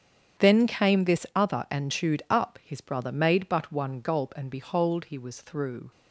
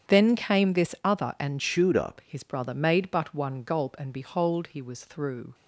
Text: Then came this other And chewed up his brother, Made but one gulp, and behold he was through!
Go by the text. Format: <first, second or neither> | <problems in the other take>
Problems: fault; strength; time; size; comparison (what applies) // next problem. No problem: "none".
first | starts louder than the rest; strong; until 1.1 s; 8.5 dB; strong in the first // changes voice from "chewed" to "up"; from 1.5 to 2.1 s; 0.6 s long